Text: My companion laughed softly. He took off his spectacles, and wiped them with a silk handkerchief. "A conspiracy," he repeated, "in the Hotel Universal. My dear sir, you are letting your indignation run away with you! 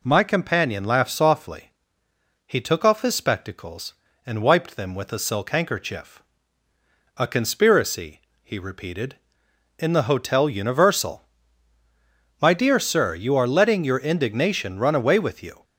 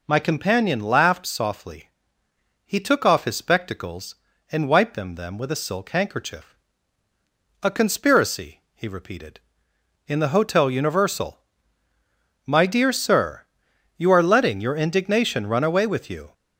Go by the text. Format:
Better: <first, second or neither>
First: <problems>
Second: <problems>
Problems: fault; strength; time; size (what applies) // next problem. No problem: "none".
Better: first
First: none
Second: says "them" twice; at 5.1 s